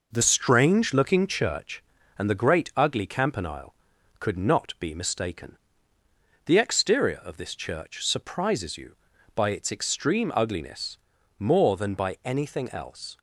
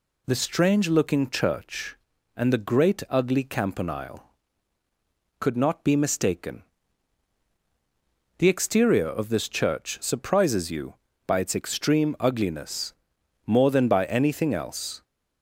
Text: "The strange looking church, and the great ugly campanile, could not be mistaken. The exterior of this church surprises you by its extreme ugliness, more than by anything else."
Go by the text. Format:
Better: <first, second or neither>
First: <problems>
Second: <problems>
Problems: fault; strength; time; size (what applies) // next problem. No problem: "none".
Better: second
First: changes voice at "strange"; from 0.2 s on; 12.9 s long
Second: none